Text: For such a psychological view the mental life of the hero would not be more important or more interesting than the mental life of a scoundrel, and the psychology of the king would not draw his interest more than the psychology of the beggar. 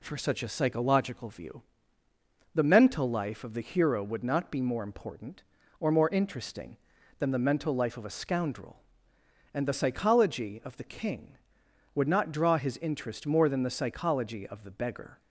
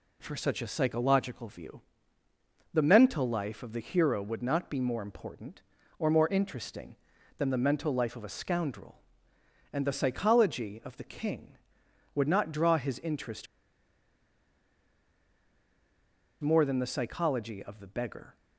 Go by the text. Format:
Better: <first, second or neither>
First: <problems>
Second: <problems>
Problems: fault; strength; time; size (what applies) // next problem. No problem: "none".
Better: first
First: pauses between "view" and "the"; noticeable; at 1.6 s; 0.92 s long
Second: pauses between "view" and "the"; noticeable; at 1.8 s; 0.92 s long // pauses between "interest" and "more"; strong; at 13.4 s; 2.9 s long